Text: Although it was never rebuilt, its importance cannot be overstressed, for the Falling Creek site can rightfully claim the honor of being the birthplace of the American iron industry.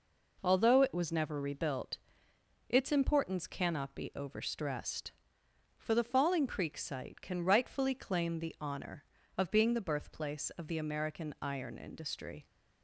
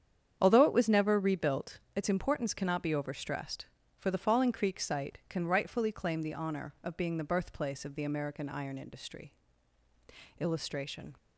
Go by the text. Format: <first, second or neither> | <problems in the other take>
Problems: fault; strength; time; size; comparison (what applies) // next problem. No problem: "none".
first | starts louder than the rest; strong; until 1.4 s; 8.5 dB // goes on to say "Illustration"; noticeable; from 10.3 s on; 0.78 s long